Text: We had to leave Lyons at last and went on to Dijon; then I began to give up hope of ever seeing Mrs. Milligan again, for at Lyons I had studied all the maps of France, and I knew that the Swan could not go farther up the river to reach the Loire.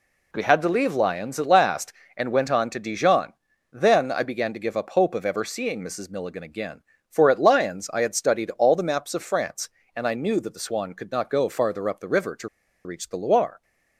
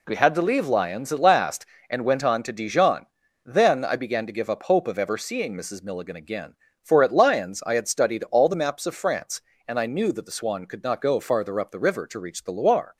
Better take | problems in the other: second | pauses between "to" and "reach"; at 12.4 s; 0.37 s long

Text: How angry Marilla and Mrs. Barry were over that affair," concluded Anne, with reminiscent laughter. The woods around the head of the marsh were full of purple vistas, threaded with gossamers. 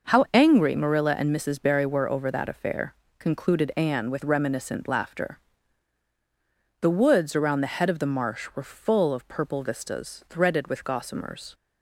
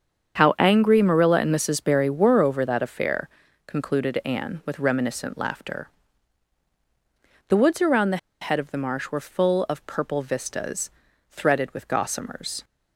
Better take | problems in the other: first | starts louder than the rest; strong; until 1.4 s; 7.5 dB // pauses between "the" and "head"; slight; at 8.1 s; 0.23 s long

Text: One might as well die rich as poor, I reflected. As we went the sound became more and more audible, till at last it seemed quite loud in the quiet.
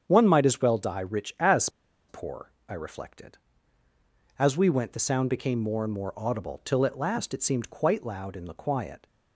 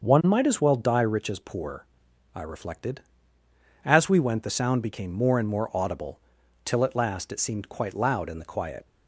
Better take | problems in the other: second | starts louder than the rest; strong; until 1.0 s; 7.5 dB; also in the second // pauses between "as" and "poor"; at 1.6 s; 0.40 s long

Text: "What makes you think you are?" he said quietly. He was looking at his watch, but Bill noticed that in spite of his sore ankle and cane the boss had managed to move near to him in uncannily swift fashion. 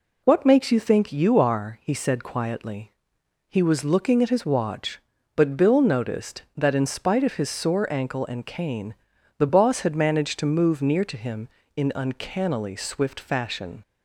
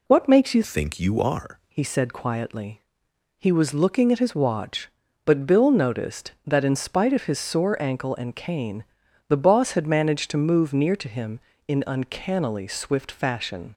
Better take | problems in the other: first | changes voice from "think" to "are"; from 0.6 to 1.5 s; 0.9 s long // pauses between "cane" and "the"; at 8.8 s; 0.44 s long; also in the first

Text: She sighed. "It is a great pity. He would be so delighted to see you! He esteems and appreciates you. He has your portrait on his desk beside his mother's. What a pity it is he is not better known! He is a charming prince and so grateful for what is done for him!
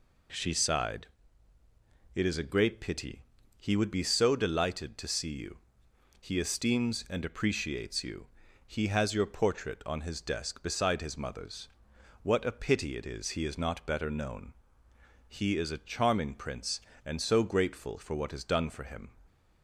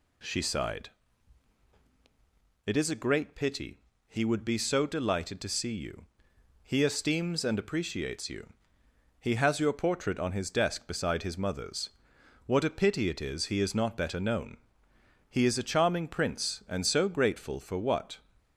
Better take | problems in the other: first | stops before "is done for him"; at 18.3 s

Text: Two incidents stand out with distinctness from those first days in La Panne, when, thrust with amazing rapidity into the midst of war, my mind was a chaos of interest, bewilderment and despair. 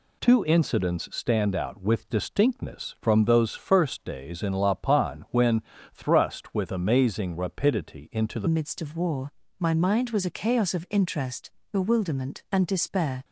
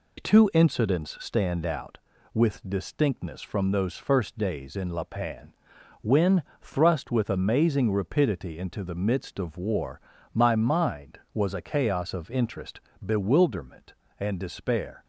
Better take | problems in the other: second | changes voice at "midst"; from 8.4 s on; 4.8 s long

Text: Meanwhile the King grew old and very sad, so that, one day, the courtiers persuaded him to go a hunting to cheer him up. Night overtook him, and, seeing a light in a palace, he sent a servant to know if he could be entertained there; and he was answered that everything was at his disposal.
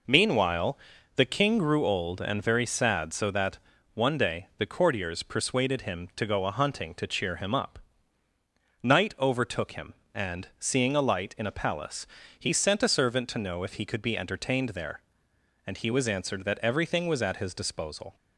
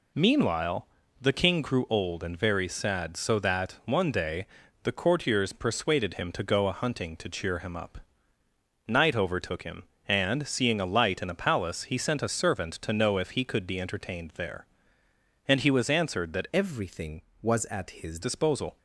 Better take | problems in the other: first | pauses between "Meanwhile" and "the"; slight; at 0.8 s; 0.34 s long; also in the first // changes voice from "everything" to "his"; from 16.5 to 18.2 s; 1.7 s long

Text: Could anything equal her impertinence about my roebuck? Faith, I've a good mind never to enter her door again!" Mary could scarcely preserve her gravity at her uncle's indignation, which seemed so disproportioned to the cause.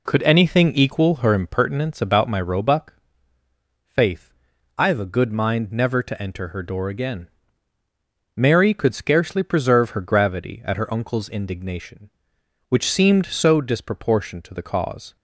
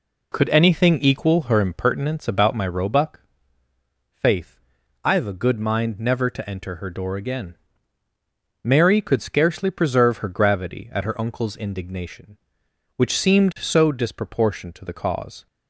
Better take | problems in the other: neither | none

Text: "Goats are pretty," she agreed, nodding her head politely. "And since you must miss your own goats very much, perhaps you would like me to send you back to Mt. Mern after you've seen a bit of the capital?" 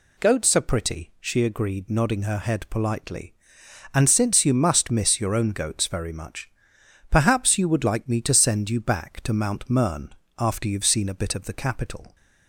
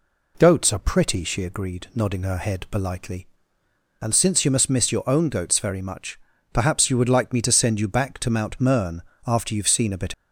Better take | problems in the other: first | pauses between "Mern" and "after"; slight; at 8.9 s; 0.26 s long; slight in the first // stops before "of the capital"; at 10.1 s

